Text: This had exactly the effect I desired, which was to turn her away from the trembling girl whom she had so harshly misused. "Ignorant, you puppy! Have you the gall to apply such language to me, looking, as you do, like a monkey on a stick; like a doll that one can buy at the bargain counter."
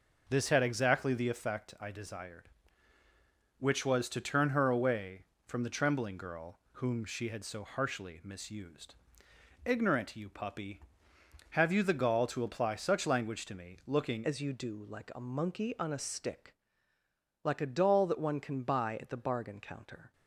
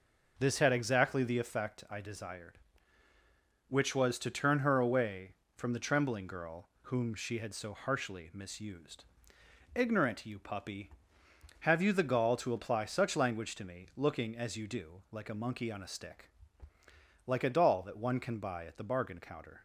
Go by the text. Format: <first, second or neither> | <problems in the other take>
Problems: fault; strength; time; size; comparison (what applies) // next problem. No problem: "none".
second | changes voice at "as"; from 14.2 s on; 5.9 s long